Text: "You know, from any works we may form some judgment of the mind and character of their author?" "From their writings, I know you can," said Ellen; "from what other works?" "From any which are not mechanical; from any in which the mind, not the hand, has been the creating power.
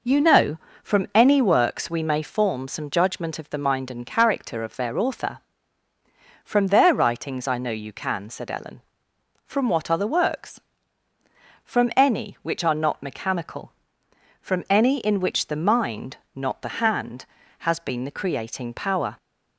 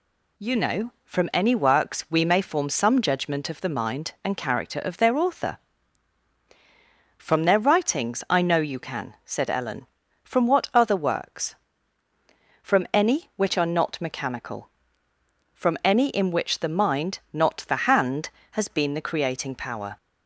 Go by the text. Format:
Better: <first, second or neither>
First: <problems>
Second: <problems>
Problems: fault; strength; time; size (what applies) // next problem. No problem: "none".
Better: neither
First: none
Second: none